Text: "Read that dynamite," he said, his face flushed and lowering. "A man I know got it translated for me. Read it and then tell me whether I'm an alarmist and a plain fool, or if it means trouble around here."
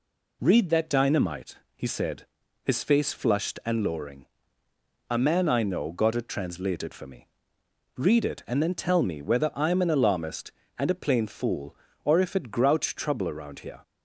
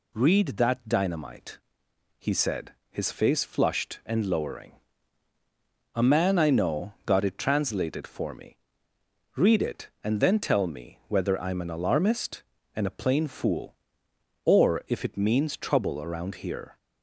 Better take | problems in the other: second | says "grouch" for "means"; at 12.5 s

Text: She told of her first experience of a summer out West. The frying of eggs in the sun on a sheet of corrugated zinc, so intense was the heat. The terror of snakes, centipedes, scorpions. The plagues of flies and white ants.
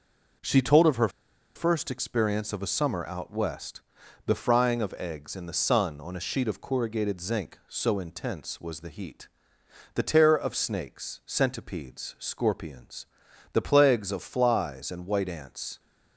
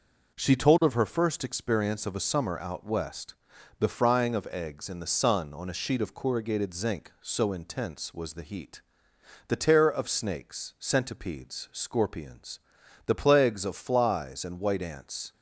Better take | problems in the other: second | pauses between "her" and "first"; noticeable; at 1.0 s; 0.46 s long

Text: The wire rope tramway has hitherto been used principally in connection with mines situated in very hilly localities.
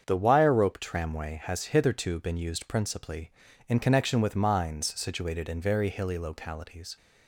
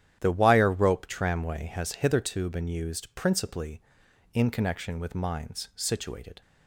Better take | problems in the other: first | starts louder than the rest; strong; until 1.2 s; 11 dB; strong in the first // stops before "in very hilly localities"; at 6.4 s

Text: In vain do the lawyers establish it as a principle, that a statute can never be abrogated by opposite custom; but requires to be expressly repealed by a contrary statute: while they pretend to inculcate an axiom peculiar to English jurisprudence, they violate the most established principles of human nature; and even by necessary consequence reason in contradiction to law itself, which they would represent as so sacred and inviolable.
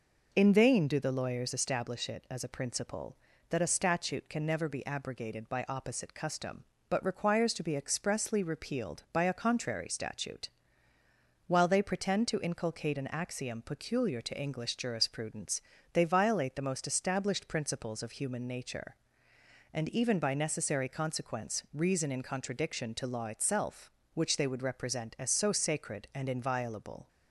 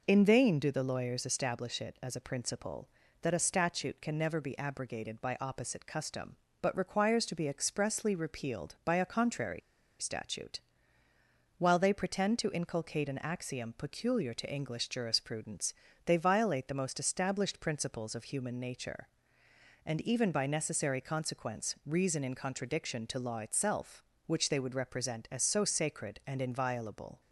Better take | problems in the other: first | pauses between "contrary" and "statute"; at 9.6 s; 0.39 s long

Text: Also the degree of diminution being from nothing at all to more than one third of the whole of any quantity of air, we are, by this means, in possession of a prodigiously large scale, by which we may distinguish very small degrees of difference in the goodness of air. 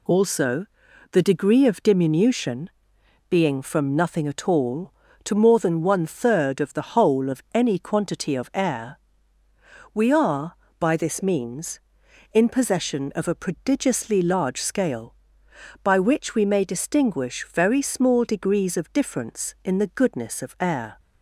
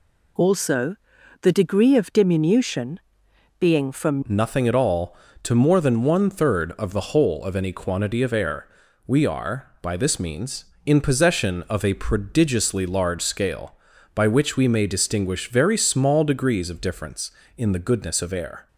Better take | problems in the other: first | pauses between "Also" and "the"; noticeable; at 0.9 s; 0.46 s long; noticeable in the first // pauses between "diminution" and "being"; noticeable; at 2.9 s; 0.60 s long; noticeable in the first // changes voice at "nothing"; from 4.2 s on; 14.4 s long

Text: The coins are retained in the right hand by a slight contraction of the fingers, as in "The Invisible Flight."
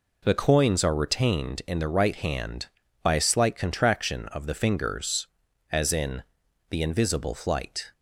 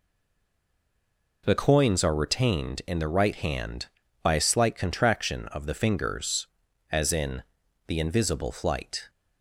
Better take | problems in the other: first | stays silent before the first word; noticeable; until 1.4 s; 1.4 s long // pauses between "in" and "The"; at 7.4 s; 0.44 s long; noticeable in the first

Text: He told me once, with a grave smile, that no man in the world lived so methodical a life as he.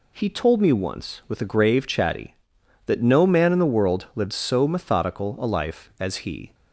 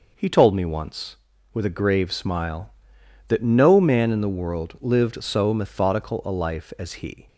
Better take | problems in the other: second | says "chatty" for "smile"; at 1.8 s

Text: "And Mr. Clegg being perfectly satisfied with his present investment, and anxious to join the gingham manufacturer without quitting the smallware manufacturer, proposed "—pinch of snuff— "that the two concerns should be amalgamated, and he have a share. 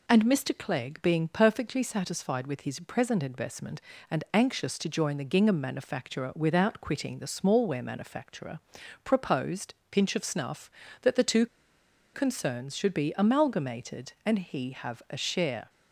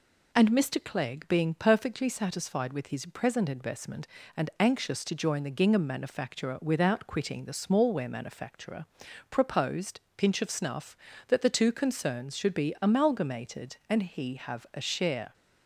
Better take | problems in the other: second | pauses between "two" and "concerns"; noticeable; at 11.4 s; 0.68 s long

